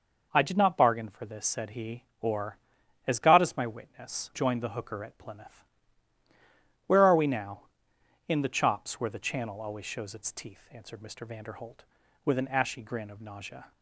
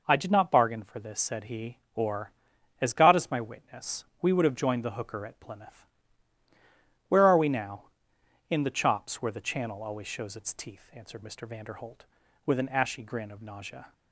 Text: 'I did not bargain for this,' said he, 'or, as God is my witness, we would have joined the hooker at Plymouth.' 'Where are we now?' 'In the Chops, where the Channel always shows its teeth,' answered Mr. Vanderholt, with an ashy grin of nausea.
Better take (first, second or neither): second